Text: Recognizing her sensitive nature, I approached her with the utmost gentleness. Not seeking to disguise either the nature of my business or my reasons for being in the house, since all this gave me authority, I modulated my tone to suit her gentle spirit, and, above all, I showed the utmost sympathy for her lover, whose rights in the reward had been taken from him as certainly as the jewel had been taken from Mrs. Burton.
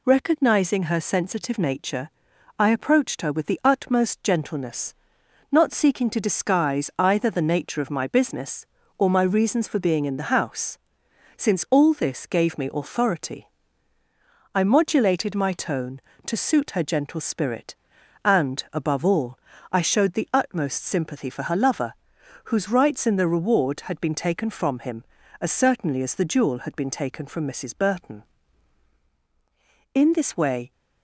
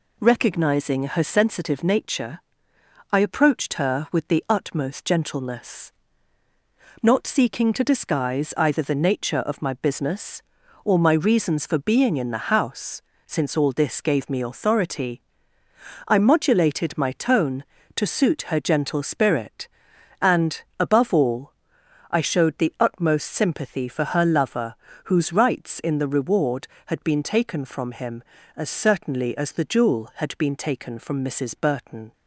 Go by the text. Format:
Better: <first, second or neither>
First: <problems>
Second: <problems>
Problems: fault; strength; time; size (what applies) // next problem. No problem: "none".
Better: second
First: goes on to say "In this way"; noticeable; from 29.9 s on; 0.78 s long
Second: none